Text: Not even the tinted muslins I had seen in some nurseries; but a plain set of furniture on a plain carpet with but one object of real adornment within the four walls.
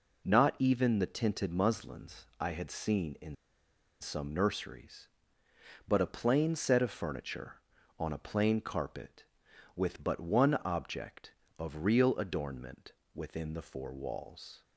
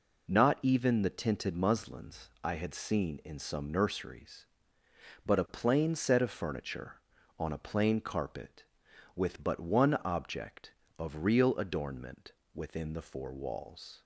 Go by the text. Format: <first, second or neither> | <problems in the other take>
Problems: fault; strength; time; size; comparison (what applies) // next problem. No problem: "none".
second | pauses between "muslins" and "I"; slight; at 2.2 s; 0.16 s long; slight in the second // pauses between "in" and "some"; noticeable; at 3.3 s; 0.67 s long // pauses between "adornment" and "within"; slight; at 12.9 s; 0.22 s long; slight in the second